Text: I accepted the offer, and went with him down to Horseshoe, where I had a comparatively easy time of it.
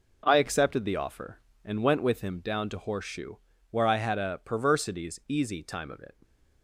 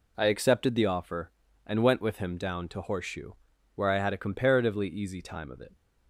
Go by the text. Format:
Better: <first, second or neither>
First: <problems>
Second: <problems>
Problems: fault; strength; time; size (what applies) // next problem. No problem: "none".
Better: second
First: says "perversities" for "comparatively"; at 4.4 s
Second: none